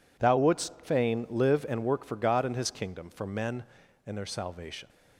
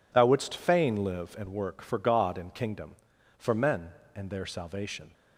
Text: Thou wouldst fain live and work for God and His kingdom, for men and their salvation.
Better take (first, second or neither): first